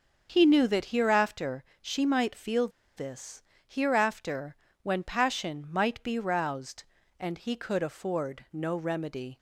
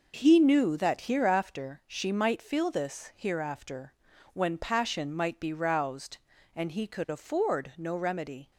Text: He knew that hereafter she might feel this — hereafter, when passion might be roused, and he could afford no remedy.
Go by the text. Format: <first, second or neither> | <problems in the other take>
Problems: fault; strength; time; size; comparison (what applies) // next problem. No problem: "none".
second | starts louder than the rest; until 1.3 s; 6.5 dB // pauses between "hereafter" and "she"; slight; at 1.6 s; 0.16 s long // pauses between "feel" and "this"; slight; at 2.6 s; 0.27 s long